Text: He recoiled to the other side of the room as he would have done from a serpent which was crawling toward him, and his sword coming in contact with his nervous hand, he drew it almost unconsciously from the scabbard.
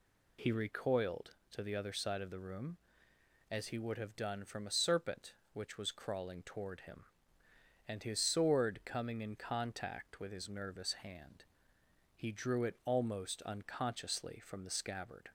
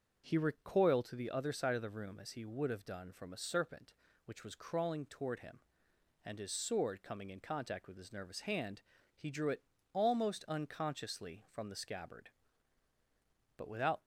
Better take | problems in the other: first | starts louder than the rest; until 1.2 s; 6.5 dB // pauses between "it" and "almost"; slight; at 9.6 s; 0.30 s long // goes on to say "But without"; slight; from 13.5 s on; 0.46 s long

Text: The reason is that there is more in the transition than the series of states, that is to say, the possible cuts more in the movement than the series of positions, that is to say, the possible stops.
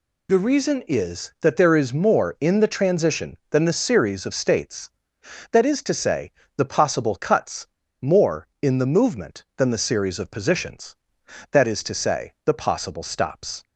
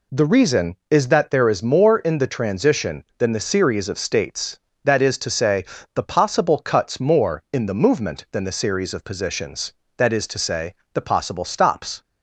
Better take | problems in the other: second | pauses between "cuts" and "more"; slight; at 7.6 s; 0.33 s long

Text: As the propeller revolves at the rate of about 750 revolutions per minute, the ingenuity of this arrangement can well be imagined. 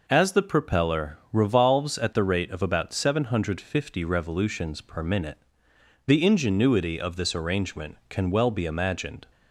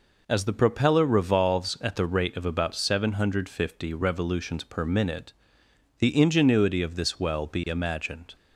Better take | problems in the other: first | skips "arrangement can"; at 7.1 s

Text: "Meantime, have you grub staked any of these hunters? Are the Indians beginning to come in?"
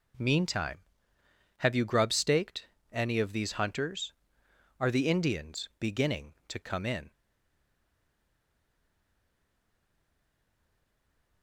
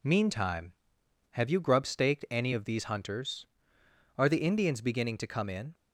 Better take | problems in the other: second | pauses between "staked" and "any"; slight; at 2.6 s; 0.24 s long // stays silent after the last word; strong; from 7.1 s on; 4.3 s long

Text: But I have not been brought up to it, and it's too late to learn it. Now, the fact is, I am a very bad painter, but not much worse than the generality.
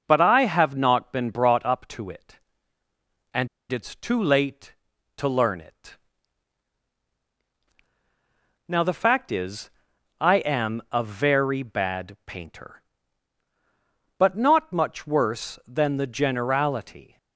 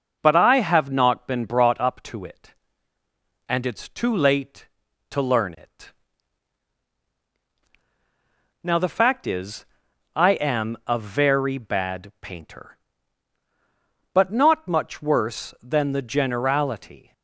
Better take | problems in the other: second | pauses between "and" and "it's"; slight; at 3.4 s; 0.23 s long

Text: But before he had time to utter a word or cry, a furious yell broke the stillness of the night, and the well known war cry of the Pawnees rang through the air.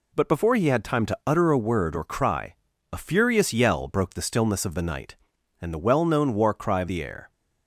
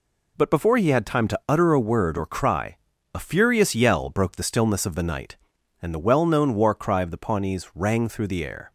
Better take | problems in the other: second | skips "the Pawnees rang through"; at 6.8 s

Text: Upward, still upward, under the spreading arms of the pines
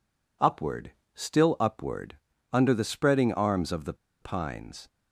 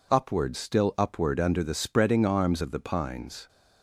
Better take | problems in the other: second | pauses between "the" and "pines"; slight; at 3.9 s; 0.26 s long

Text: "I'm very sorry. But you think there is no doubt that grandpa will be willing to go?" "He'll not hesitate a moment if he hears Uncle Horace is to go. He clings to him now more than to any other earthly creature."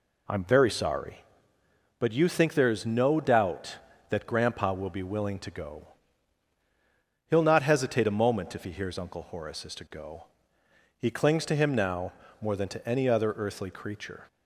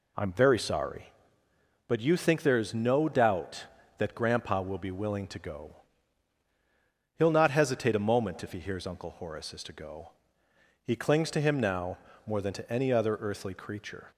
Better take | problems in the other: neither | pauses between "now" and "more"; slight; the same in both

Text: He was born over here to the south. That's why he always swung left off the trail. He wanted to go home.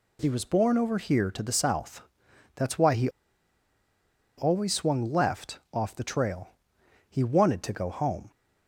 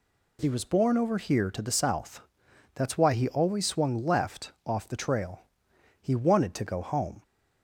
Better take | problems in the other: second | pauses between "he" and "always"; strong; at 3.0 s; 1.2 s long

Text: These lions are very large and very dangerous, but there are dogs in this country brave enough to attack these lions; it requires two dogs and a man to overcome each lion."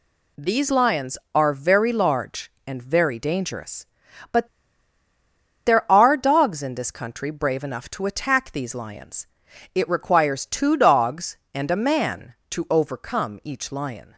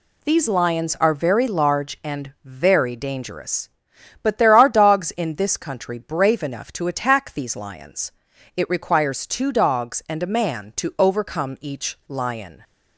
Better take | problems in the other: second | pauses between "but" and "there"; at 4.4 s; 1.1 s long

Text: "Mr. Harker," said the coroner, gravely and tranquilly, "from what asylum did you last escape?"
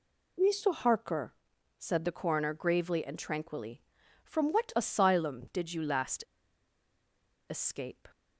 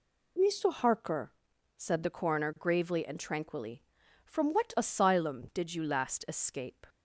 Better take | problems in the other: second | pauses between "last" and "escape"; strong; at 6.2 s; 1.2 s long

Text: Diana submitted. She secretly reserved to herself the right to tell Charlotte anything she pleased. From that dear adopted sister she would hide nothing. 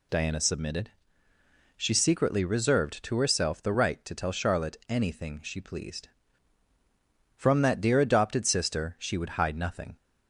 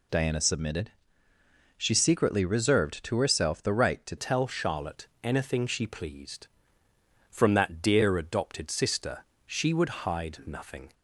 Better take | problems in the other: first | changes voice at "tell"; from 4.1 s on; 6.8 s long // pauses between "Charlotte" and "anything"; slight; at 5.0 s; 0.18 s long // pauses between "sister" and "she"; slight; at 9.2 s; 0.20 s long

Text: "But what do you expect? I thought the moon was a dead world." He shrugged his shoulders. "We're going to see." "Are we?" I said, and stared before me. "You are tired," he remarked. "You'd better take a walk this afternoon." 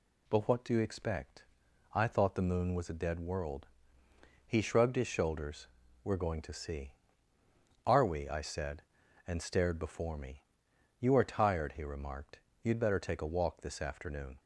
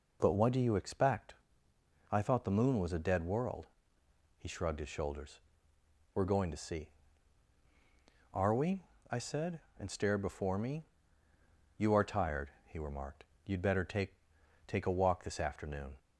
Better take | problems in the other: first | says "take" twice; at 14.6 s

